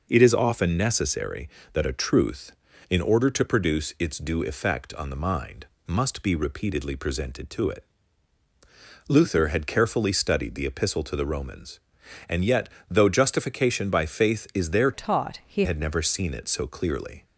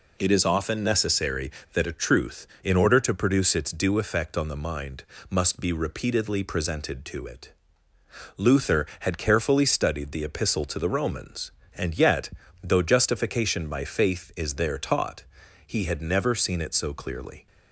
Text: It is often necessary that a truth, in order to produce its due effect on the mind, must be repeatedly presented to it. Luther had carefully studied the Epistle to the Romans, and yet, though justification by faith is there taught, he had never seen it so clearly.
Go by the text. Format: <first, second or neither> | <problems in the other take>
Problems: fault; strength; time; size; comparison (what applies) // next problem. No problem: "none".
second | changes voice from "taught" to "he"; from 14.9 to 15.6 s; 0.7 s long